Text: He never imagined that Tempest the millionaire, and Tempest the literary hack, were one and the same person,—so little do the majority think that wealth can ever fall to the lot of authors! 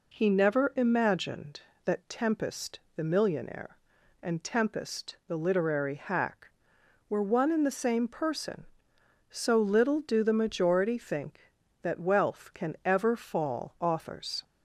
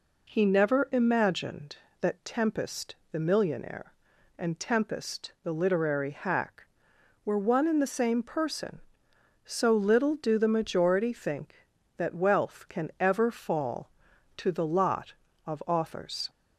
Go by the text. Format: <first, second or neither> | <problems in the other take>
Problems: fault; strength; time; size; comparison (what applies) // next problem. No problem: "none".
second | pauses between "Tempest" and "the"; slight; at 2.8 s; 0.16 s long; slight in the second // skips "to the lot of"; at 13.7 s